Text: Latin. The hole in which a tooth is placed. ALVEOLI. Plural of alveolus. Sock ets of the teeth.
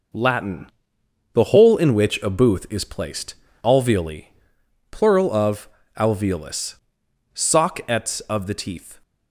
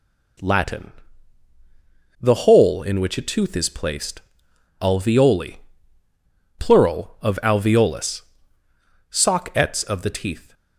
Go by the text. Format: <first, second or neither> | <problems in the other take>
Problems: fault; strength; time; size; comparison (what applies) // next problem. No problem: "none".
second | says "booth" for "tooth"; at 2.2 s // pauses between "of" and "alveolus"; slight; at 5.6 s; 0.28 s long